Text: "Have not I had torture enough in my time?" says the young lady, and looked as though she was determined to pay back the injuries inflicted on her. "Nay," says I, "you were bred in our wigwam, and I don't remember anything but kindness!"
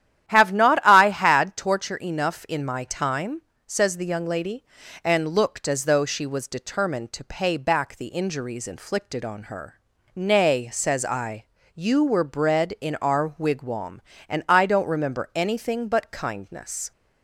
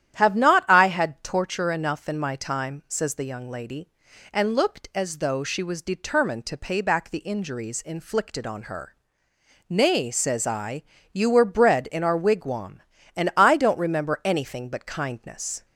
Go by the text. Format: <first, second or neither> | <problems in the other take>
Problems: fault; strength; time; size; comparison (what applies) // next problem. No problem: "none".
neither | starts louder than the rest; strong; the same in both